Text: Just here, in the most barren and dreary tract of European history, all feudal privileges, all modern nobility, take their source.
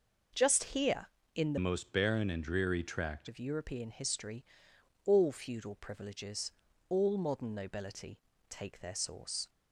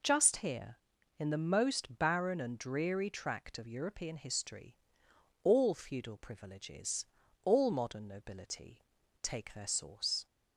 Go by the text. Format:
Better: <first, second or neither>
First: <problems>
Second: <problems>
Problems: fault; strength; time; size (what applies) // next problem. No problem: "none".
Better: second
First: changes voice from "most" to "tract"; from 1.5 to 3.2 s; 1.7 s long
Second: none